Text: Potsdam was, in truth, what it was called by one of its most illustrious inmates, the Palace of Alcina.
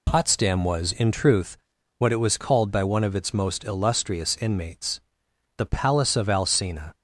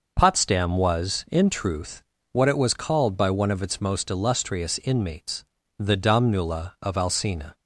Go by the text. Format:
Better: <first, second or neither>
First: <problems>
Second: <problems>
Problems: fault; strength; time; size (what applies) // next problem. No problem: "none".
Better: first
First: none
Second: says "Domnula" for "Palace"; at 5.9 s